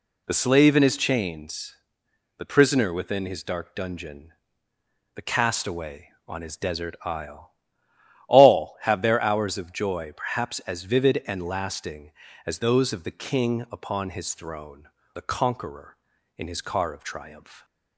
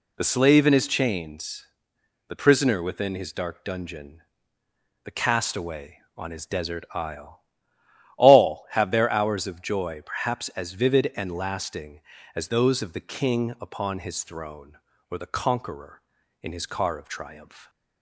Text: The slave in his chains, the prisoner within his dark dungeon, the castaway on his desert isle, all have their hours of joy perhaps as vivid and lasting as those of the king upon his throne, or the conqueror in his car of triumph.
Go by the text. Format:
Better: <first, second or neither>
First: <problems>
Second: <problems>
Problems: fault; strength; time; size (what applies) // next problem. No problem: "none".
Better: second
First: skips "or"; at 15.0 s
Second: none